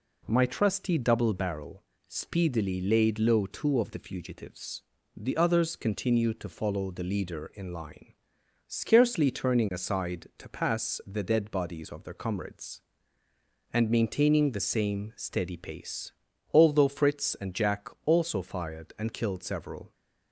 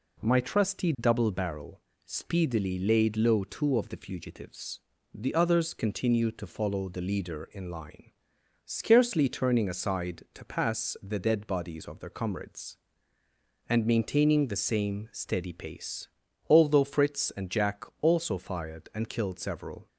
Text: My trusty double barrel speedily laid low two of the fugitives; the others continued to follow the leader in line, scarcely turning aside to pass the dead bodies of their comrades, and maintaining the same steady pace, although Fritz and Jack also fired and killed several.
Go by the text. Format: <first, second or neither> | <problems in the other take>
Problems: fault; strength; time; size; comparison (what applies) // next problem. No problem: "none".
neither | pauses between "barrel" and "speedily"; slight; the same in both // pauses between "Jack" and "also"; slight; the same in both